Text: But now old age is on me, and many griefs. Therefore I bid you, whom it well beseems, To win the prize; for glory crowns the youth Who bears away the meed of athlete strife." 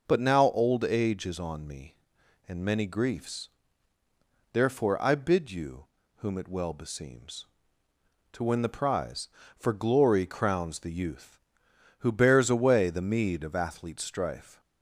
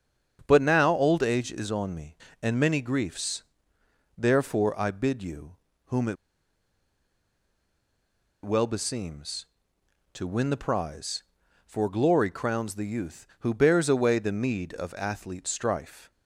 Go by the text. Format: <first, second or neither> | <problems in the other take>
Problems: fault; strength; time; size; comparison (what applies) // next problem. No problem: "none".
first | starts louder than the rest; strong; until 1.4 s; 8 dB // pauses between "it" and "well"; strong; at 6.1 s; 2.2 s long